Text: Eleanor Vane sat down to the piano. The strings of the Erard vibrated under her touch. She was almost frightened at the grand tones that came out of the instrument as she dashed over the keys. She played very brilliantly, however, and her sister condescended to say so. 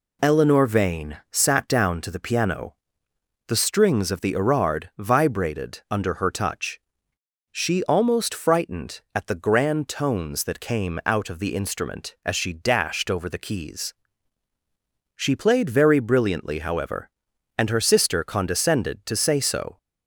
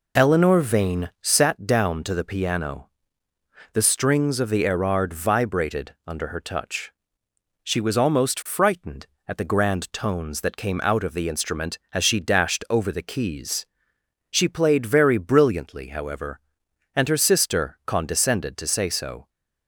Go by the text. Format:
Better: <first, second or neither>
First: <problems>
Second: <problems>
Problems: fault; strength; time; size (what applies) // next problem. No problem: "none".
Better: second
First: skips "was"; at 7.8 s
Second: none